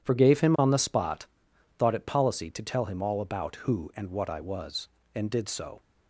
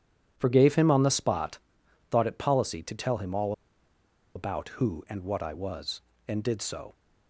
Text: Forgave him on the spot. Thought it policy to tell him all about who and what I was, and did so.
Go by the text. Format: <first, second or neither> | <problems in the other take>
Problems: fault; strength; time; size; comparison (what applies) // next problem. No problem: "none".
first | pauses between "all" and "about"; noticeable; at 3.5 s; 0.83 s long